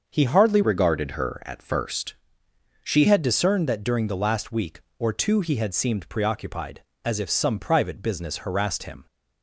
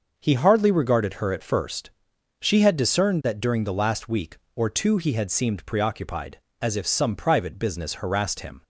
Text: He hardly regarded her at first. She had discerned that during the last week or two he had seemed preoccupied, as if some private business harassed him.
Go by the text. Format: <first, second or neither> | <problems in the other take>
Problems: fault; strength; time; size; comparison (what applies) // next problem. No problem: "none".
second | starts louder than the rest; until 1.1 s; 6 dB // changes voice from "regarded" to "She"; from 0.6 to 3.0 s; 2.4 s long